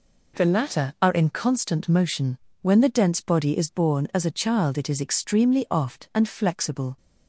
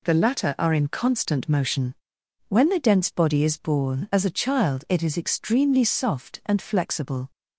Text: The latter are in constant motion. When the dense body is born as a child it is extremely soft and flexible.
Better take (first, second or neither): second